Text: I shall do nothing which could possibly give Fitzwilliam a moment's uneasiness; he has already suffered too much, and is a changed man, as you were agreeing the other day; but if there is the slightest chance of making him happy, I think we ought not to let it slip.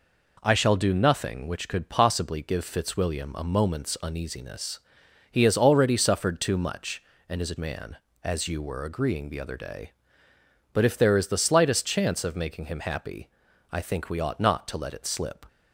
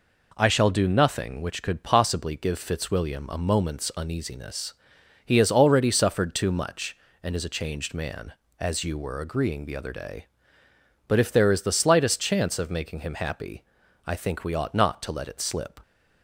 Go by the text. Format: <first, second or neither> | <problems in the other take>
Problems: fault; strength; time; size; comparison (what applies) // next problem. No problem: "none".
second | skips "changed"; at 7.5 s